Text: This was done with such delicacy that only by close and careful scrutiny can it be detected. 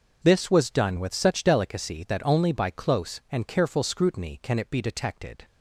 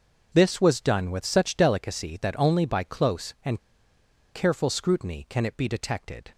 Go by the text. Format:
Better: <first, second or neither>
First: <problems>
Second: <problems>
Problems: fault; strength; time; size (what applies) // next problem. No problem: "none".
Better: first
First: none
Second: pauses between "and" and "careful"; noticeable; at 3.5 s; 0.73 s long